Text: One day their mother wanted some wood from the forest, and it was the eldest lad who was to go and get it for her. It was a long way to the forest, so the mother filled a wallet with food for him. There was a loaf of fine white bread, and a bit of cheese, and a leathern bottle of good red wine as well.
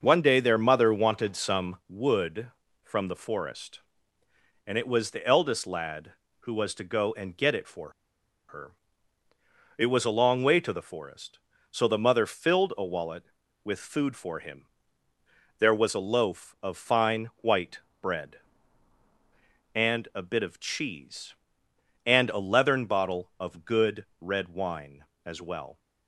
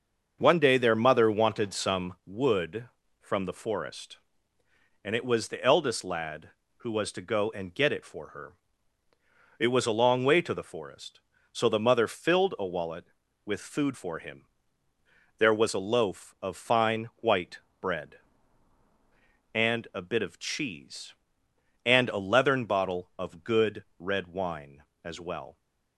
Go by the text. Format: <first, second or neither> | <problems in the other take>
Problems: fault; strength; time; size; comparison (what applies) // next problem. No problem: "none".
second | starts louder than the rest; until 1.0 s; 6.5 dB; also in the second // pauses between "for" and "her"; noticeable; at 7.8 s; 0.58 s long // pauses between "white" and "bread"; slight; at 17.7 s; 0.24 s long; slight in the second